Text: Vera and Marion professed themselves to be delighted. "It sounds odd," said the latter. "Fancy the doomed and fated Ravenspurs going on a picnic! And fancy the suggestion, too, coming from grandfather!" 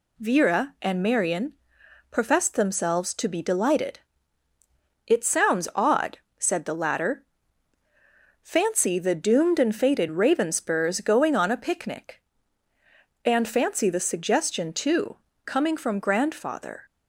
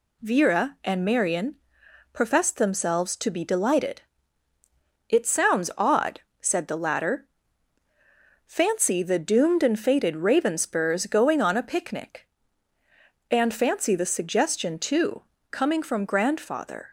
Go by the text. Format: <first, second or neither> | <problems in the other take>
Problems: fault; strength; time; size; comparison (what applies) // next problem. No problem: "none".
neither | pauses between "Marion" and "professed"; noticeable; the same in both